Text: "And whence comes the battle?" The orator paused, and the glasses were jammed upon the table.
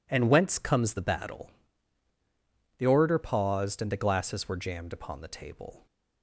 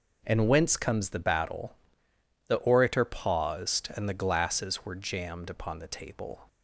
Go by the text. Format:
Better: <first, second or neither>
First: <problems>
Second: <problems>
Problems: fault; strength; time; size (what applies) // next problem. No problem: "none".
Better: neither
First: none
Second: none